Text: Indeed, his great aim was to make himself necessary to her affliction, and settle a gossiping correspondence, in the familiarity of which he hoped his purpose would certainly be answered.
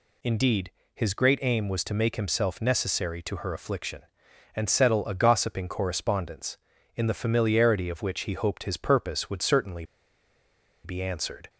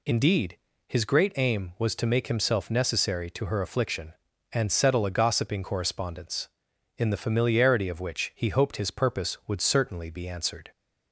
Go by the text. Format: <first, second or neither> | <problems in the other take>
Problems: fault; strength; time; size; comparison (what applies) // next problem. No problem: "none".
second | pauses between "certainly" and "be"; at 9.8 s; 0.99 s long